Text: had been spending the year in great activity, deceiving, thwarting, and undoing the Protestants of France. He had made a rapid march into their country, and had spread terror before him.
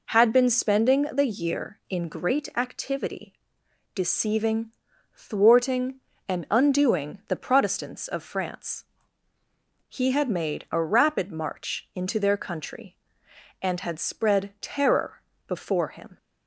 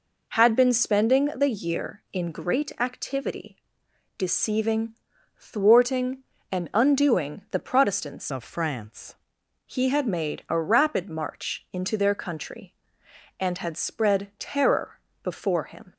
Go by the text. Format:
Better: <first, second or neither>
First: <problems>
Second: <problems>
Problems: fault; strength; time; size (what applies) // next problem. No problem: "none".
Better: first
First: pauses between "terror" and "before"; slight; at 15.2 s; 0.26 s long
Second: changes voice from "of" to "France"; from 8.3 to 9.1 s; 0.8 s long // pauses between "terror" and "before"; slight; at 14.9 s; 0.24 s long